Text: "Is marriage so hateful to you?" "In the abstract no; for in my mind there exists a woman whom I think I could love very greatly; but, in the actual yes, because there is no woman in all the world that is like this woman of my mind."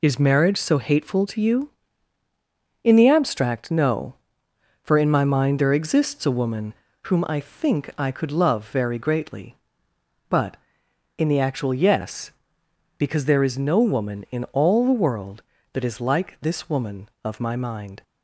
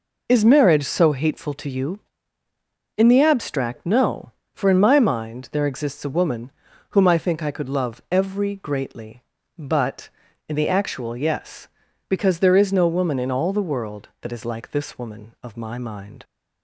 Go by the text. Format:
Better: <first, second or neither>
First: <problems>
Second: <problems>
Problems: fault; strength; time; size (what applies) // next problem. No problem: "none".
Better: first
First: pauses between "woman" and "whom"; slight; at 6.7 s; 0.30 s long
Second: pauses between "woman" and "whom"; at 6.4 s; 0.42 s long // says "every" for "very"; at 8.0 s